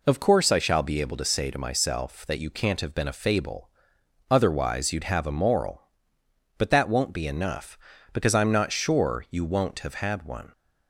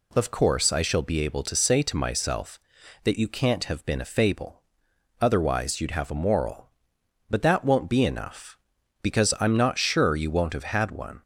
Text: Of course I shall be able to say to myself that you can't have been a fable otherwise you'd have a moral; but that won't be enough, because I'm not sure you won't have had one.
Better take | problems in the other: neither | pauses between "fable" and "otherwise"; noticeable; the same in both

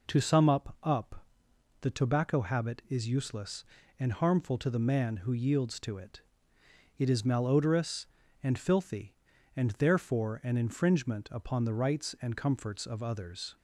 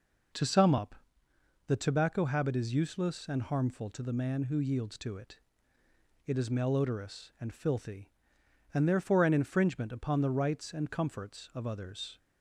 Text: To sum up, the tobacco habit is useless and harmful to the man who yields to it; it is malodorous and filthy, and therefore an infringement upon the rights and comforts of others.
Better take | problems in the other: second | says "up" twice; at 0.8 s

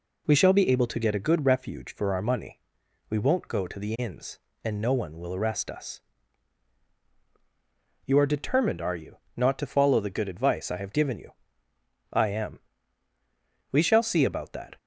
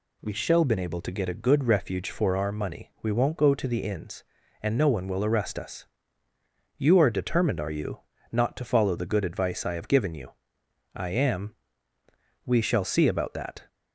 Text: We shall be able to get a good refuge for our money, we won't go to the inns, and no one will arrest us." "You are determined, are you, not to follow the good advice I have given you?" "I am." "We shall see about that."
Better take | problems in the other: first | says "been" for "be"; at 0.6 s

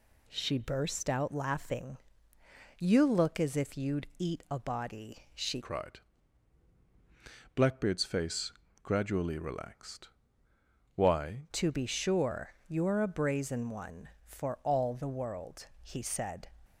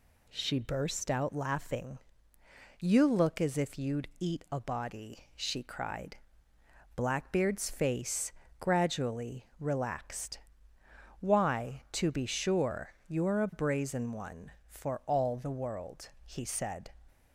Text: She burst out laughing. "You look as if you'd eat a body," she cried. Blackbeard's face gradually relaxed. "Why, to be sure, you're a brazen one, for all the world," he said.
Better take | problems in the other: second | changes voice from "cried" to "Why"; from 5.6 to 11.4 s; 5.8 s long // pauses between "face" and "gradually"; slight; at 8.5 s; 0.32 s long; slight in the second

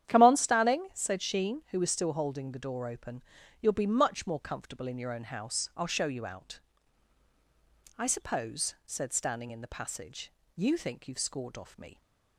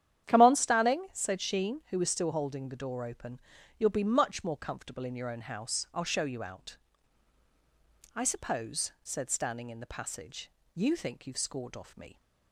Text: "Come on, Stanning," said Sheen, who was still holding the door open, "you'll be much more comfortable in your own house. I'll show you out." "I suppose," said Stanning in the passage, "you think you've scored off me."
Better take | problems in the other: neither | starts louder than the rest; strong; the same in both

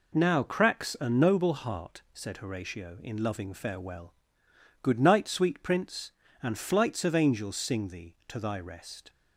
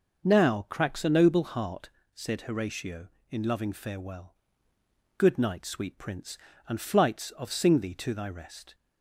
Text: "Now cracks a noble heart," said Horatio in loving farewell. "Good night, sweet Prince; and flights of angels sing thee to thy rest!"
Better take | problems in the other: first | starts louder than the rest; noticeable; until 1.3 s; 6 dB // skips "angels"; at 7.5 s

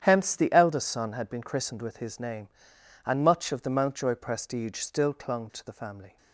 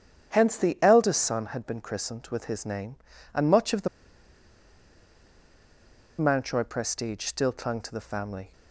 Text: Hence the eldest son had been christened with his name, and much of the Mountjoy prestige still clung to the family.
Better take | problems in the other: first | starts louder than the rest; strong; until 1.3 s; 8.5 dB; strong in the first // pauses between "the" and "Mountjoy"; strong; at 3.8 s; 2.3 s long

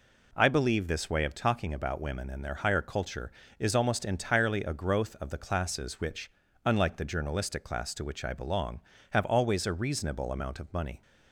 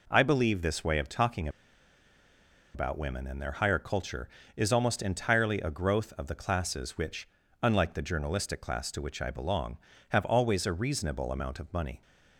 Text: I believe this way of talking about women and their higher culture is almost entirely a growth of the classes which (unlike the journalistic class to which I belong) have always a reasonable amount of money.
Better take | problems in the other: first | pauses between "talking" and "about"; strong; at 1.4 s; 1.2 s long

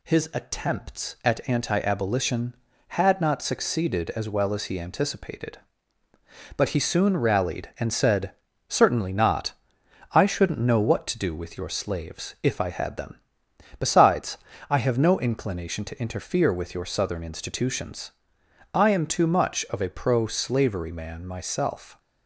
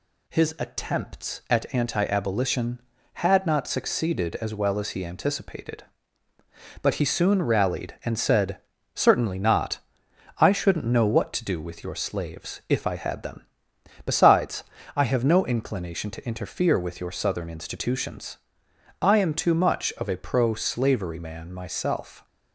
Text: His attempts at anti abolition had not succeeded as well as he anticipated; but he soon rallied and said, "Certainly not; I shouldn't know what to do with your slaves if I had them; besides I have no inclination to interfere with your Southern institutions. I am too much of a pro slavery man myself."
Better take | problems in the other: neither | pauses between "besides" and "I"; slight; the same in both

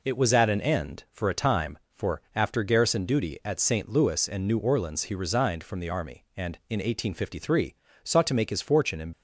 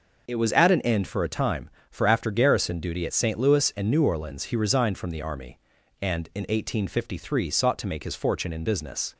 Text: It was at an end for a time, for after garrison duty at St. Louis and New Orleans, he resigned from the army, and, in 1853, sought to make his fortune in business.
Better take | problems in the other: second | stops before "business"; at 9.1 s

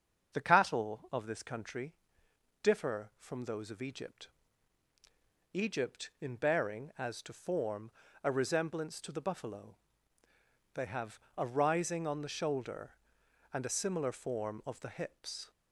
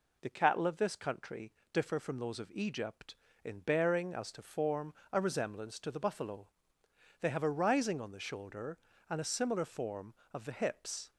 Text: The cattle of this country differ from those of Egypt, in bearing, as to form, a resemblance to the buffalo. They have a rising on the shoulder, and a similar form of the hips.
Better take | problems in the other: second | starts louder than the rest; until 1.3 s; 7 dB // pauses between "country" and "differ"; noticeable; at 1.9 s; 0.68 s long; slight in the second // says "Egypt" twice; at 5.5 s // pauses between "have" and "a"; slight; at 11.1 s; 0.20 s long

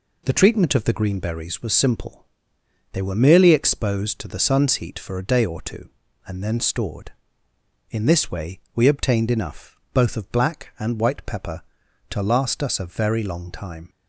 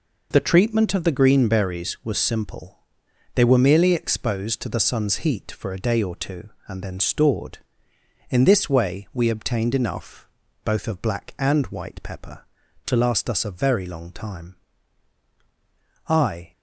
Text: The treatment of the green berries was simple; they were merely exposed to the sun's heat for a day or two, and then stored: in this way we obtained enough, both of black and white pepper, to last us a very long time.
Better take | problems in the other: first | goes on to say "I"; slight; from 16.0 s on; 0.44 s long

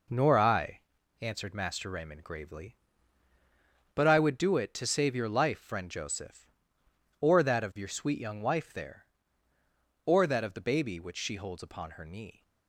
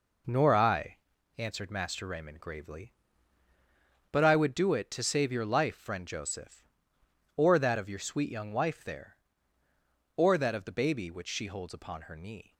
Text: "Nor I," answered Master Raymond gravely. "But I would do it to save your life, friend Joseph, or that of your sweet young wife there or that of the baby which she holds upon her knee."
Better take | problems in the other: neither | none

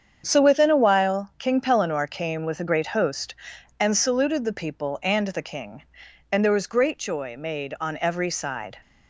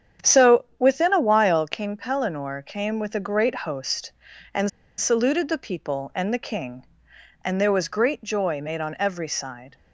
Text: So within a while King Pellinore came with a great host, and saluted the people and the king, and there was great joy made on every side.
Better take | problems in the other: first | starts louder than the rest; strong; until 1.3 s; 8.5 dB; strong in the first // pauses between "and" and "saluted"; slight; at 4.6 s; 0.28 s long

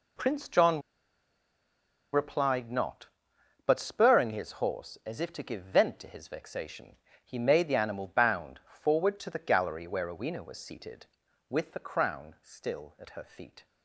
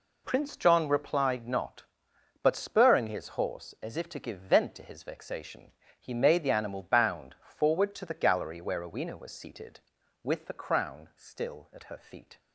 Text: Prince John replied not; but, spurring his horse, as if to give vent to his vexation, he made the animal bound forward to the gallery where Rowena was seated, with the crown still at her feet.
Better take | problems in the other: second | pauses between "John" and "replied"; strong; at 0.8 s; 1.3 s long

